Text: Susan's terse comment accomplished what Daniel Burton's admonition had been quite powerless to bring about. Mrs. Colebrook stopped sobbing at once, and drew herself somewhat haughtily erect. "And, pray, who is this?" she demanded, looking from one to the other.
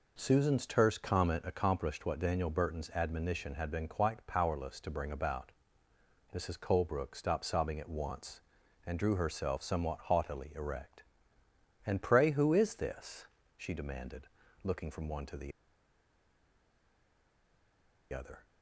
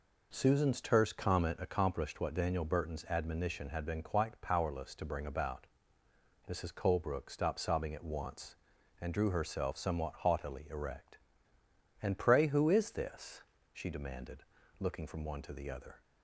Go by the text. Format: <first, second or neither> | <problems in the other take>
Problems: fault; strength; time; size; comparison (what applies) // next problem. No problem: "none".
second | pauses between "the" and "other"; strong; at 15.5 s; 2.6 s long